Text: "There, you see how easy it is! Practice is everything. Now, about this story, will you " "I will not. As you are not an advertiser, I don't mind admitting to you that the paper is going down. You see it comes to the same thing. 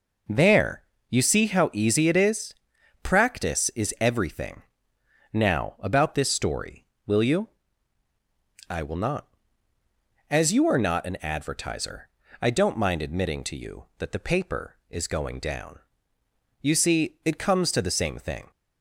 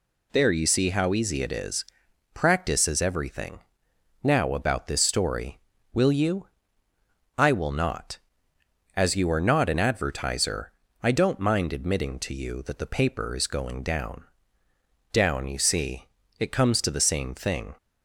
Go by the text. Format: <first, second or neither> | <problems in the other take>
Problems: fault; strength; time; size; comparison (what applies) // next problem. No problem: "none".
first | says "down" twice; at 15.1 s // pauses between "see" and "it"; slight; at 16.0 s; 0.32 s long